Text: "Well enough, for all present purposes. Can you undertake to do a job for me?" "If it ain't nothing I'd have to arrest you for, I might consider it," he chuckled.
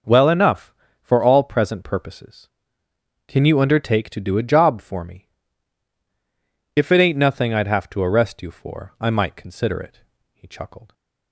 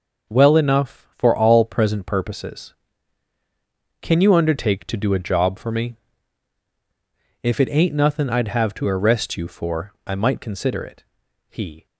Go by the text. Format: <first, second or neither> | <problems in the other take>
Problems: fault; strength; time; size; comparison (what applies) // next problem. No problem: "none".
first | stops before "chuckled"; at 11.8 s